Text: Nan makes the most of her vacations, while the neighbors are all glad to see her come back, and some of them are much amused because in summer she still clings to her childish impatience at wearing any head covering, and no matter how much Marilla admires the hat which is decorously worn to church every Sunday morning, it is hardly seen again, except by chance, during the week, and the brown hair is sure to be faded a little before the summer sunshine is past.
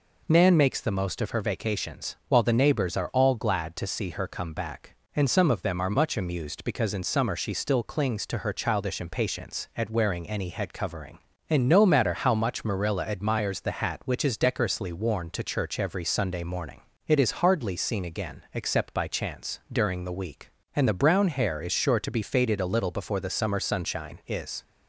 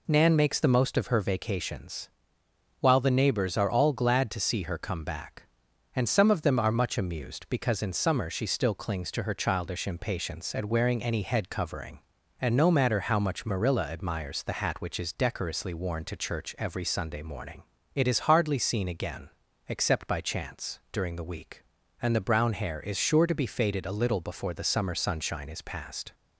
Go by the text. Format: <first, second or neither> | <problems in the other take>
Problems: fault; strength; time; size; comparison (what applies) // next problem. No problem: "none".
second | stops before "past"; at 24.6 s